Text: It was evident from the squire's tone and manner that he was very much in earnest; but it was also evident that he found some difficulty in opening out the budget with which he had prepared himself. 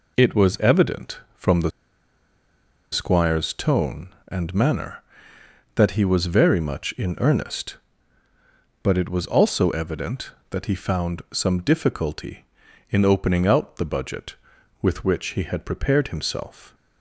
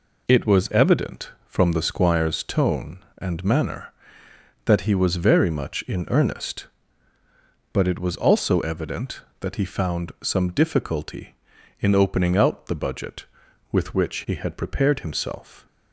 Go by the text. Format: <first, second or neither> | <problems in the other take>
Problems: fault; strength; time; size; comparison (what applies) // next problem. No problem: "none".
second | pauses between "the" and "squire's"; at 1.7 s; 1.2 s long